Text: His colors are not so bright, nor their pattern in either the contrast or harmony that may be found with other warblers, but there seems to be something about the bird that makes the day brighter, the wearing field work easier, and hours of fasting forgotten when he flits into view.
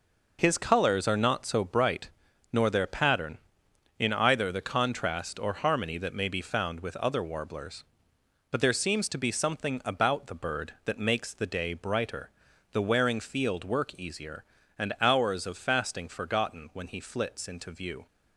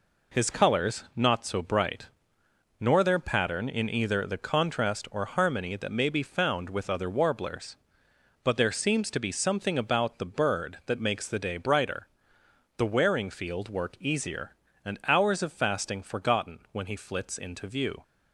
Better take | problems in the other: first | skips "are"; at 1.0 s

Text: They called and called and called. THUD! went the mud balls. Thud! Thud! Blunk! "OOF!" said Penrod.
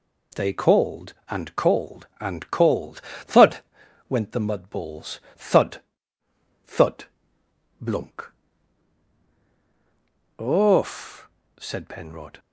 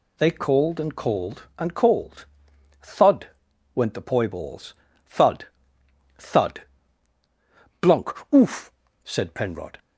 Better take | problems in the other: first | says "poi" for "mud"; at 4.0 s

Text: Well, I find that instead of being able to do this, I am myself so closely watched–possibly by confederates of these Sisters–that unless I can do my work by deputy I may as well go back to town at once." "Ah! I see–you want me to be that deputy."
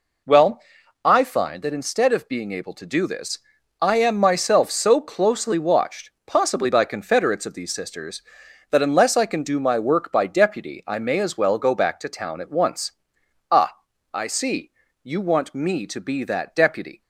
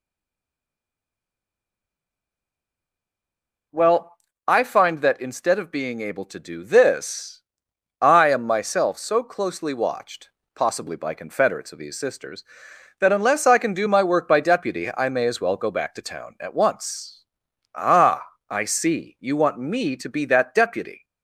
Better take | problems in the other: first | stays silent before the first word; strong; until 3.7 s; 3.7 s long

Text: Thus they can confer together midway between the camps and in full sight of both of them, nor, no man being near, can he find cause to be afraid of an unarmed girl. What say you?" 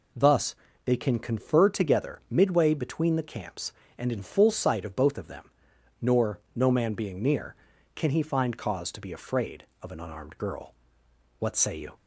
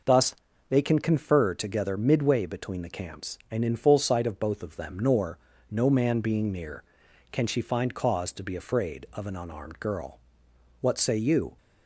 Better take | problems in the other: first | pauses between "Thus" and "they"; slight; at 0.3 s; 0.34 s long; slight in the first // says "she" for "he"; at 7.4 s

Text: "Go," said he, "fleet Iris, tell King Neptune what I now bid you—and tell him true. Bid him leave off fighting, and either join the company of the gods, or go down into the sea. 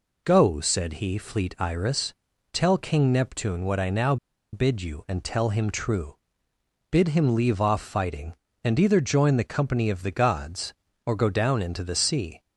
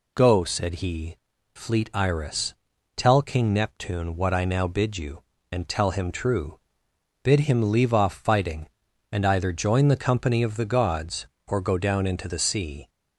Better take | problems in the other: second | pauses between "now" and "bid"; at 4.1 s; 0.37 s long

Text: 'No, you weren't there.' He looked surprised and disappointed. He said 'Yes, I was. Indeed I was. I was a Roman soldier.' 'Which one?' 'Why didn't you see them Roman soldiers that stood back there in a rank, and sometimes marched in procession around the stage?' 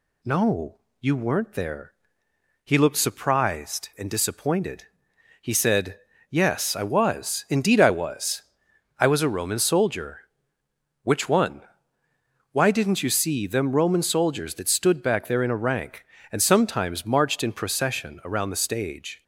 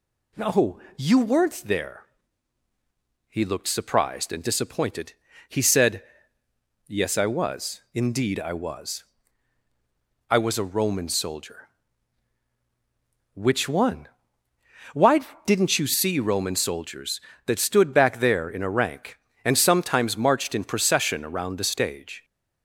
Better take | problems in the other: first | pauses between "said" and "Yes"; noticeable; at 6.0 s; 0.84 s long; slight in the first // pauses between "Why" and "didn't"; slight; at 15.2 s; 0.24 s long // skips "them"; at 16.1 s

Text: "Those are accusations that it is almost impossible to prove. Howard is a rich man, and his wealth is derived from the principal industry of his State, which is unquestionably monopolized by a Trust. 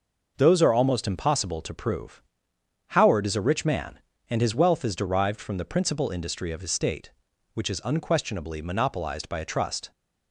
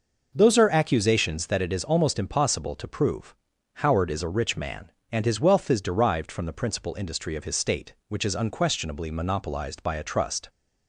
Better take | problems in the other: second | skips "accusations that it is"; at 0.7 s

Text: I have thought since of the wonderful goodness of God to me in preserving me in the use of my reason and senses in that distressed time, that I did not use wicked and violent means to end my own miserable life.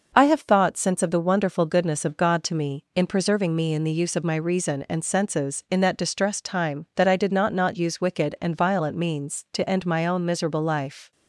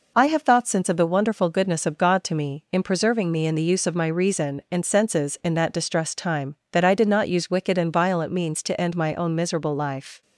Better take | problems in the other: second | says "not" twice; at 7.5 s

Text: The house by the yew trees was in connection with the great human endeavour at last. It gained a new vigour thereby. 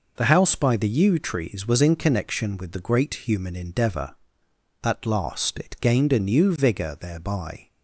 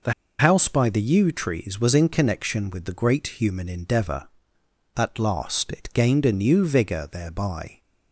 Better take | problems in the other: first | pauses between "The" and "house"; slight; at 0.1 s; 0.26 s long

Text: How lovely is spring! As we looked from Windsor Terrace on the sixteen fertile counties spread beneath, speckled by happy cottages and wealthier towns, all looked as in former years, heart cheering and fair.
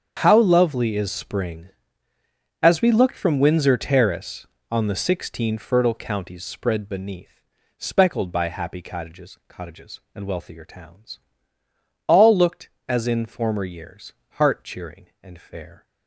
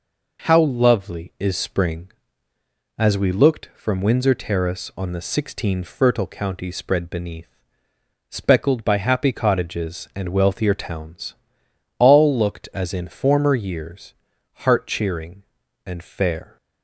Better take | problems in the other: second | starts louder than the rest; strong; until 1.2 s; 7.5 dB // says "cottages" twice; at 9.4 s

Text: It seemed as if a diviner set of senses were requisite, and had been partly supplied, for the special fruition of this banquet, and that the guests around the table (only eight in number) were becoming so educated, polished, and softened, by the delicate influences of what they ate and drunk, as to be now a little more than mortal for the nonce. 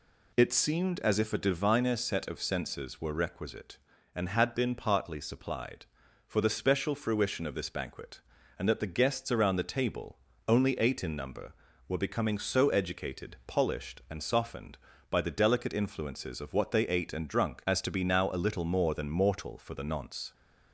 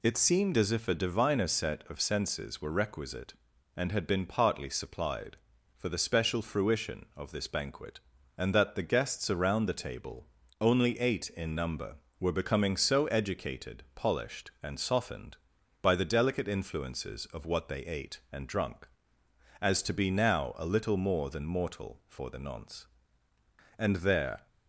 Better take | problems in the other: first | goes on to say "And there"; noticeable; from 23.7 s on; 0.70 s long

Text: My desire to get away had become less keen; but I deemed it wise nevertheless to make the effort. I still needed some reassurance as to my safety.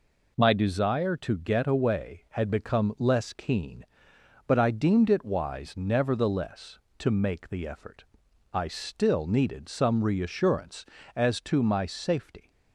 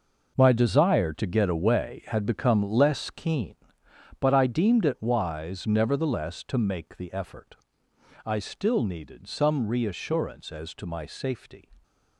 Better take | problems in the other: first | gets quieter; strong; throughout; 11.5 dB

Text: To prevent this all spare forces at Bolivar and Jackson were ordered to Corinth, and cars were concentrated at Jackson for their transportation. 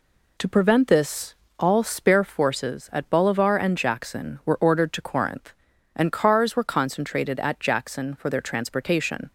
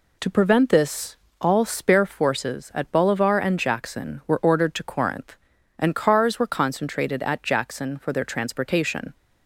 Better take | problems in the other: neither | pauses between "this" and "all"; slight; the same in both

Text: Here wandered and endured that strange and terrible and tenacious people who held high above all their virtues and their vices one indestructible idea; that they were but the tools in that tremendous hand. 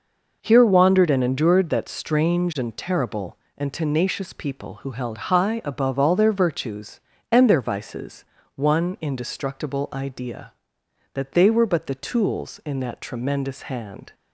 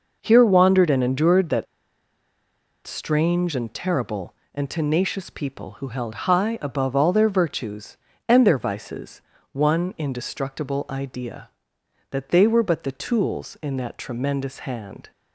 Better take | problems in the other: first | pauses between "that" and "strange"; at 1.6 s; 1.2 s long // pauses between "vices" and "one"; slight; at 9.2 s; 0.32 s long; slight in the first

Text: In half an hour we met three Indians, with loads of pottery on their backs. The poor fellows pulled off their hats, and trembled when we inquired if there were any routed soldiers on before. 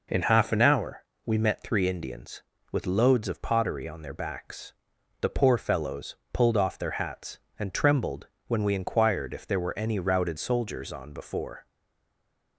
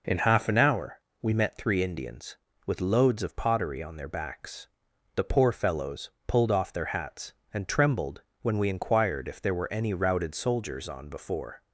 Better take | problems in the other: second | pauses between "hour" and "we"; slight; at 1.0 s; 0.20 s long; slight in the second // pauses between "fellows" and "pulled"; slight; at 6.1 s; 0.18 s long; slight in the second // pauses between "trembled" and "when"; slight; at 8.2 s; 0.22 s long; slight in the second // stays silent after the last word; slight; from 11.6 s on; 0.9 s long

